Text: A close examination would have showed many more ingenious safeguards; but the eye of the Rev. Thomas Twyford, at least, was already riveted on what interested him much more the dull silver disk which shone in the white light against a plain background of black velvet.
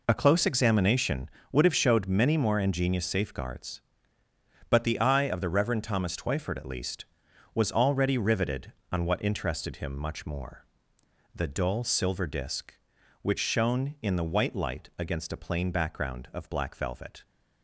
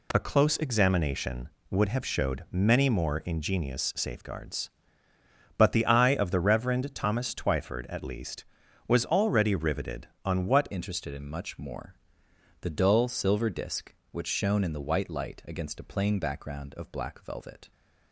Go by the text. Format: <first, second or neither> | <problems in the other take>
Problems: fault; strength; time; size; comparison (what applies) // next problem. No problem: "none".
first | changes voice at "interested"; from 10.7 s on; 7.0 s long // pauses between "more" and "the"; noticeable; at 11.9 s; 0.66 s long; noticeable in the first